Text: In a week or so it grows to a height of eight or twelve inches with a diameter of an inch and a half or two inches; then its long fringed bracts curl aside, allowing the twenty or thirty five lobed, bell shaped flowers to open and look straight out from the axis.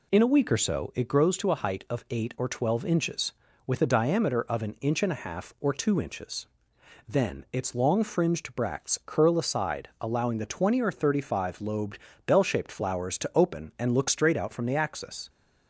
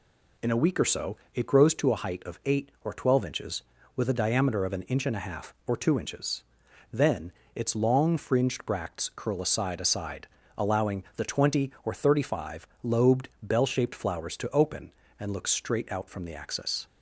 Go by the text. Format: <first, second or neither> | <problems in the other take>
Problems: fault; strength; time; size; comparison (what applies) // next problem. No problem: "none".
first | pauses between "so" and "it"; slight; at 1.1 s; 0.18 s long // pauses between "then" and "its"; slight; at 7.3 s; 0.24 s long // says "aside" twice; at 9.7 s // pauses between "five" and "lobed"; slight; at 12.6 s; 0.16 s long